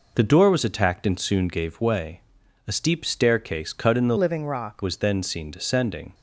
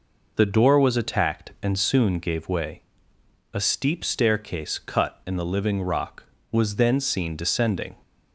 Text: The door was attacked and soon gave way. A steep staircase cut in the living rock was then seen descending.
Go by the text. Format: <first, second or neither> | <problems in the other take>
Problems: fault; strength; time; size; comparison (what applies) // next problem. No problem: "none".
second | changes voice from "living" to "rock"; from 4.1 to 4.8 s; 0.7 s long